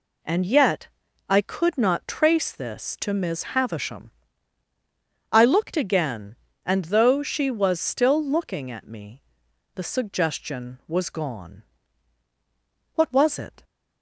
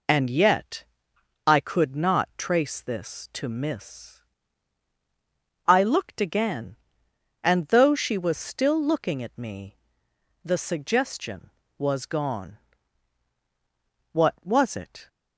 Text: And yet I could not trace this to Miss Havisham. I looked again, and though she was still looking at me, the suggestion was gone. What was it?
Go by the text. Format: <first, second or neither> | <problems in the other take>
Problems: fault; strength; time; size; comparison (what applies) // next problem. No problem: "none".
first | pauses between "yet" and "I"; noticeable; at 0.8 s; 0.62 s long; also in the first // skips "Havisham"; at 4.9 s